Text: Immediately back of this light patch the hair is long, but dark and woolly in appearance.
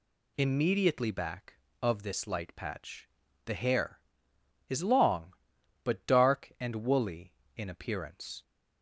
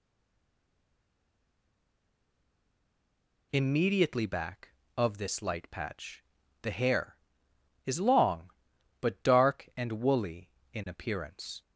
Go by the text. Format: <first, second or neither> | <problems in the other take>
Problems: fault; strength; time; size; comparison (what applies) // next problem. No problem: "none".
first | stays silent before the first word; strong; until 3.5 s; 3.5 s long // pauses between "patch" and "the"; at 6.2 s; 0.38 s long; also in the first